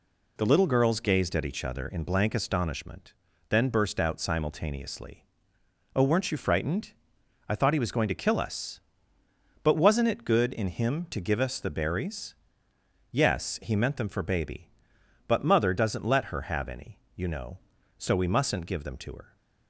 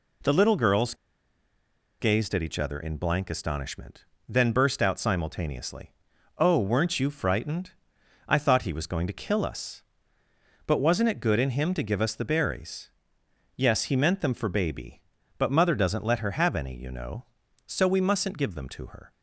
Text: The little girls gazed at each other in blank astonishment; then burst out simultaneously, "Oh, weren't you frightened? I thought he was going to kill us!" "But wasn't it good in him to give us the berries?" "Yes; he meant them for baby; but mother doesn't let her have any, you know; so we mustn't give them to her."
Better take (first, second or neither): first